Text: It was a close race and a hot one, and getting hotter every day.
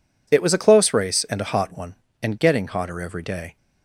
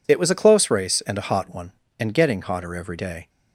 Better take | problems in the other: neither | none

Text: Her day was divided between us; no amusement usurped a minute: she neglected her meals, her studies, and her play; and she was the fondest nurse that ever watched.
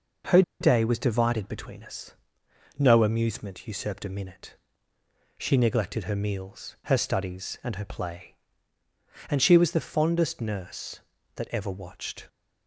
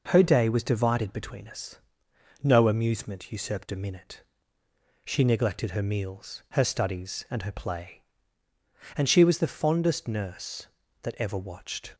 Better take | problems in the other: second | pauses between "Her" and "day"; slight; at 0.4 s; 0.19 s long

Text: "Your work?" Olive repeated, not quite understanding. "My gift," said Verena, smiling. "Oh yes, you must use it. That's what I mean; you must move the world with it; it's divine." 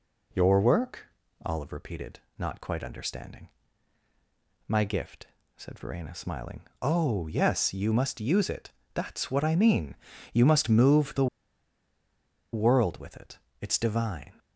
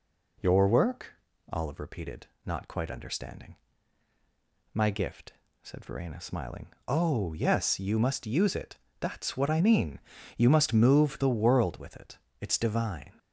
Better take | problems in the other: second | pauses between "the" and "world"; strong; at 11.2 s; 1.2 s long

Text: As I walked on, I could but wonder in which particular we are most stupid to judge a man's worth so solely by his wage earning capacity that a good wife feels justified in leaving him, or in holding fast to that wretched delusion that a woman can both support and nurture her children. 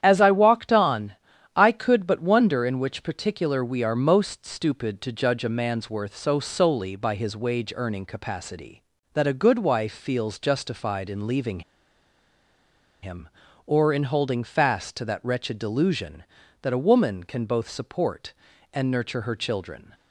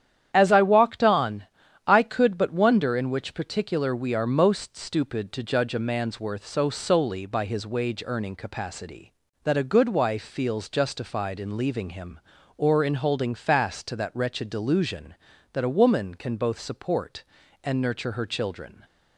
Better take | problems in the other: second | starts louder than the rest; strong; until 1.0 s; 10 dB; strong in the second // pauses between "leaving" and "him"; strong; at 11.6 s; 1.4 s long

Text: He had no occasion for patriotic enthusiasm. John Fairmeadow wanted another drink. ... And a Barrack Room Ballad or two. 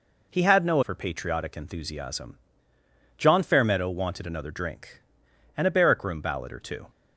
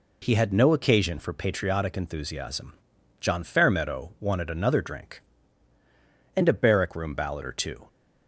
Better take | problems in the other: second | skips "occasion"; at 0.8 s

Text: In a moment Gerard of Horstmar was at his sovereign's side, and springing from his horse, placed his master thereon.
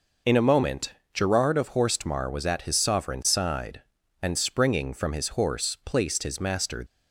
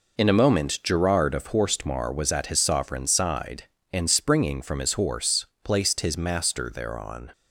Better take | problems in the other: second | pauses between "moment" and "Gerard"; slight; at 0.9 s; 0.22 s long // stops before "thereon"; at 6.8 s

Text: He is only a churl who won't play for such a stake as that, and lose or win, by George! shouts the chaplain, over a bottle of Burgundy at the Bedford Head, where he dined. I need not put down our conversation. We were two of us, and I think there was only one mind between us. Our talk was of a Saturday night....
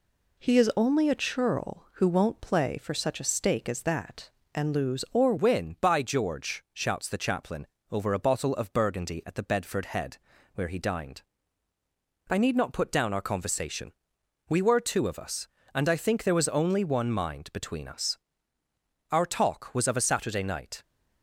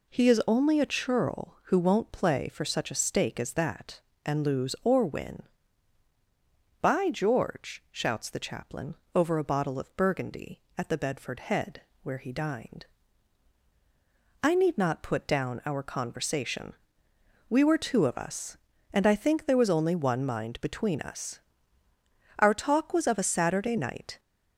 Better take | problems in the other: second | changes voice at "win"; from 5.3 s on; 15.5 s long

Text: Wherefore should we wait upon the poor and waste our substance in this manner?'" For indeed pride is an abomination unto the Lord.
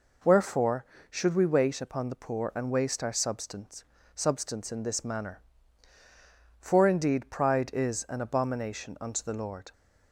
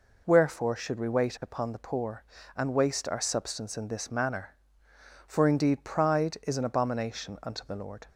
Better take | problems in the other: second | says "substance" twice; at 4.1 s

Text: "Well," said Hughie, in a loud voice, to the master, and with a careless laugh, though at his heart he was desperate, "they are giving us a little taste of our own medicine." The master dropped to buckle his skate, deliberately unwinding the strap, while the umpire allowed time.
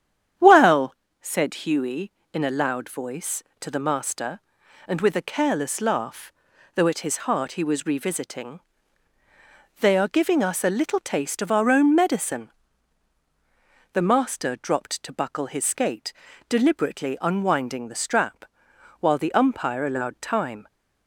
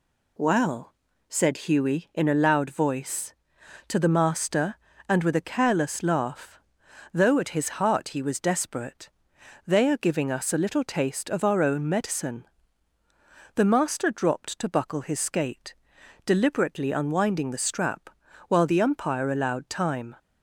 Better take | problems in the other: second | starts louder than the rest; strong; until 1.6 s; 9 dB // says "revisiting" for "desperate"; at 7.8 s

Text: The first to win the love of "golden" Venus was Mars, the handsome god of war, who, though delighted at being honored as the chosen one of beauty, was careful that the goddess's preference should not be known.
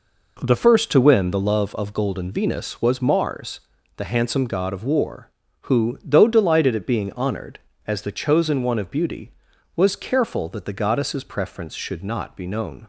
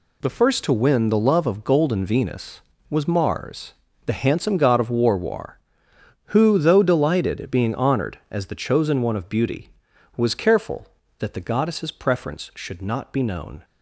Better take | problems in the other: first | says "war" twice; at 5.1 s

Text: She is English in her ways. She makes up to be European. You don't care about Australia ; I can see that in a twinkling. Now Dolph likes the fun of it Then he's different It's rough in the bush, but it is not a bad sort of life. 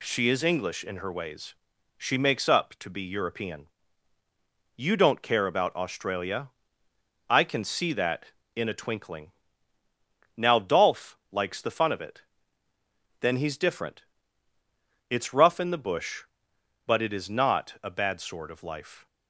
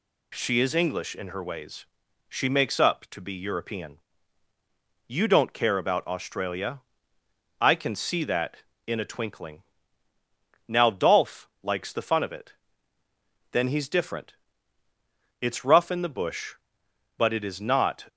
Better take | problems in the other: first | pauses between "it" and "Then"; noticeable; at 12.5 s; 0.98 s long; noticeable in the first // pauses between "different" and "It's"; at 14.3 s; 1.0 s long; also in the first // stops before "a bad sort of life"; at 18.0 s

